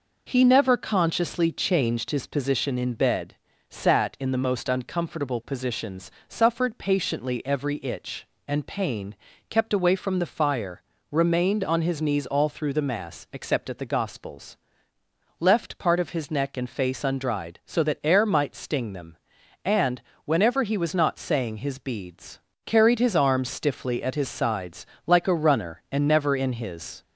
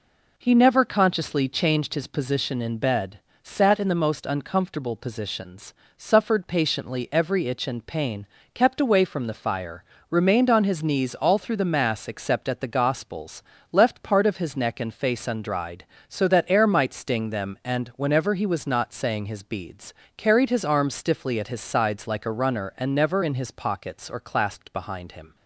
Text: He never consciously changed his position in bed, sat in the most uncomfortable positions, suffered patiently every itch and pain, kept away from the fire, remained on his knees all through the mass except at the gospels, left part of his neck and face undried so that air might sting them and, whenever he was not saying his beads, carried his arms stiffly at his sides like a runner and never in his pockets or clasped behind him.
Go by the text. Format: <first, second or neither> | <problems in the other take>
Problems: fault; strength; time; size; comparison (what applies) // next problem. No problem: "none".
second | pauses between "sides" and "like"; slight; at 24.8 s; 0.22 s long // stops before "pockets or clasped behind him"; at 27.0 s